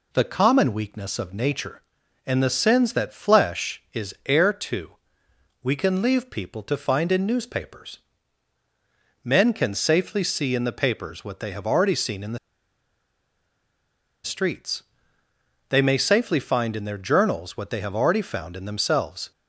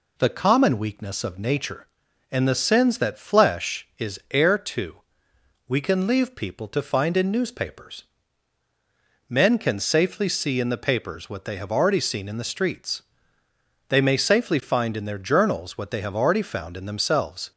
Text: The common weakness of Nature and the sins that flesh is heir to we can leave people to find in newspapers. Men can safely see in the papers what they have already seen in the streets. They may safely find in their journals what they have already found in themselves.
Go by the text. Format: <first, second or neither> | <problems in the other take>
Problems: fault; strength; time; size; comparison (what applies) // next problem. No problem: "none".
second | pauses between "to" and "we"; noticeable; at 4.9 s; 0.72 s long; noticeable in the second // pauses between "the" and "streets"; strong; at 12.3 s; 1.8 s long